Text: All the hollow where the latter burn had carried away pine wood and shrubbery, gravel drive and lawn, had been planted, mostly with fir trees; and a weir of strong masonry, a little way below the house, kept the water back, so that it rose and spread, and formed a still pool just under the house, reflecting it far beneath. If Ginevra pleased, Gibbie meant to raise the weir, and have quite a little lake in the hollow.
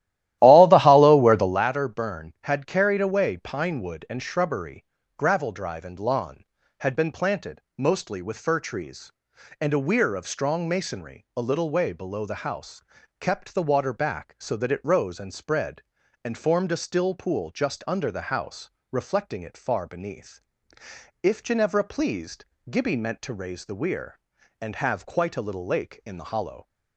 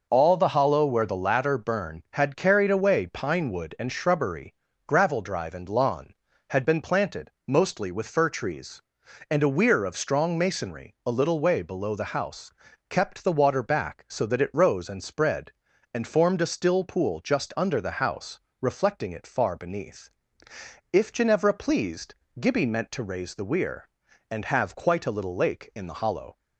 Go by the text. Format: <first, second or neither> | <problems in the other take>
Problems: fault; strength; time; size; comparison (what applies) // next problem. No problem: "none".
second | starts louder than the rest; strong; until 1.7 s; 14.5 dB